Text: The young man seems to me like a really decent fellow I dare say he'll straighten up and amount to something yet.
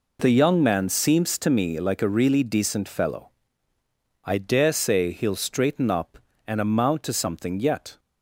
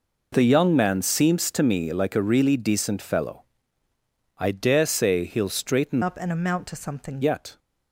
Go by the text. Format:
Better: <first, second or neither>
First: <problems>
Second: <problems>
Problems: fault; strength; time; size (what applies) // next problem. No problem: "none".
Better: first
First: pauses between "fellow" and "I"; noticeable; at 3.2 s; 0.92 s long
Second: pauses between "fellow" and "I"; noticeable; at 3.4 s; 0.92 s long // changes voice from "up" to "something"; from 6.0 to 7.2 s; 1.2 s long